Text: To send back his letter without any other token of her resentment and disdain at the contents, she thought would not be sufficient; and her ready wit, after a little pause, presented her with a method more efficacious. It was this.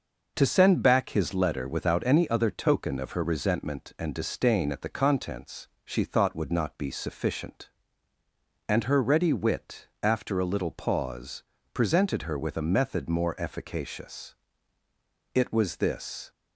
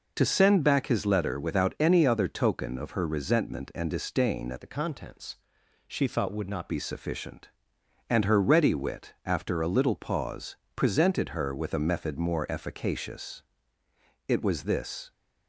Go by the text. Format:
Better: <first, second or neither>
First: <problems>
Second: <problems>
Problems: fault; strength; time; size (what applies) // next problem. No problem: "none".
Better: first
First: none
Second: changes voice from "the" to "not"; from 4.6 to 6.7 s; 2.1 s long